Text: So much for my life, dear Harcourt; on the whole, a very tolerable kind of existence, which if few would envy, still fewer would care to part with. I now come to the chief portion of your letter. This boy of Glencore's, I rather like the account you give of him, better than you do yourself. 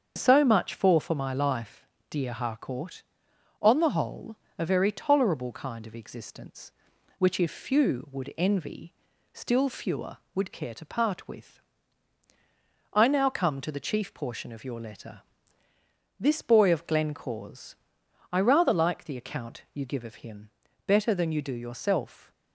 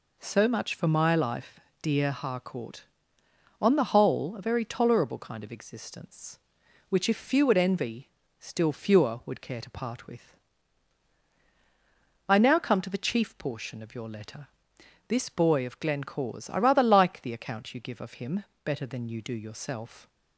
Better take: second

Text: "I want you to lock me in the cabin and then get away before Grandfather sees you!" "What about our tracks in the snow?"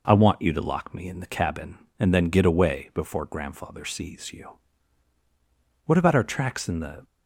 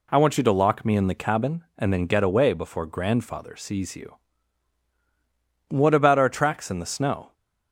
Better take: second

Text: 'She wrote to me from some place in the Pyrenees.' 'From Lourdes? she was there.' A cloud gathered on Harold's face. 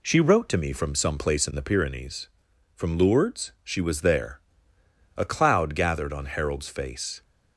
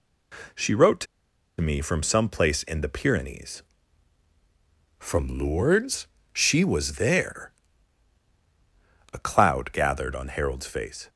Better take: first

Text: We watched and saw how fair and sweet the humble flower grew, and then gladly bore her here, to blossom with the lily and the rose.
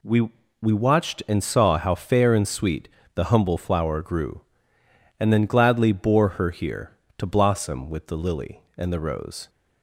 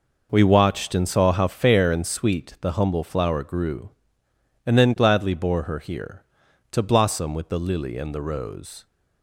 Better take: second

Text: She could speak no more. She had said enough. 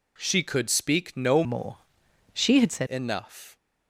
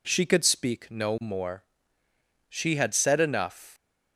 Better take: second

